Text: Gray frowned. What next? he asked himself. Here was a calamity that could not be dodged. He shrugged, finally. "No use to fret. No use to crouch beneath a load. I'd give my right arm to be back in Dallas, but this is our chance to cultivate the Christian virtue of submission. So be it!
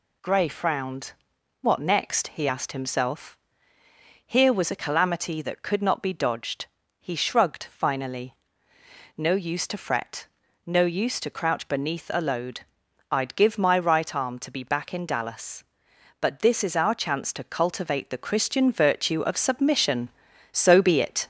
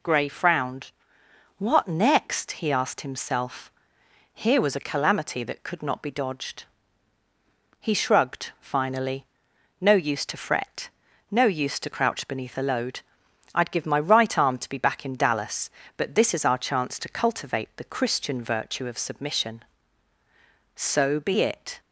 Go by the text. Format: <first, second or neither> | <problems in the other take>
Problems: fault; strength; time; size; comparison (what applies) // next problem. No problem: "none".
neither | none